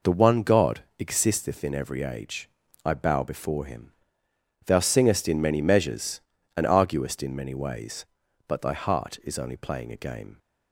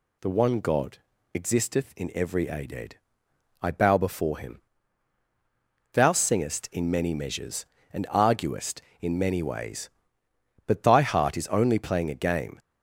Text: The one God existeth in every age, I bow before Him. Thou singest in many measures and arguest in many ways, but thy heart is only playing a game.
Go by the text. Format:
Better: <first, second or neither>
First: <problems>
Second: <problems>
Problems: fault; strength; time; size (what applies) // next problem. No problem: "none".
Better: first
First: pauses between "God" and "existeth"; slight; at 0.8 s; 0.16 s long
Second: pauses between "God" and "existeth"; slight; at 0.9 s; 0.36 s long // says "aded" for "age"; at 2.4 s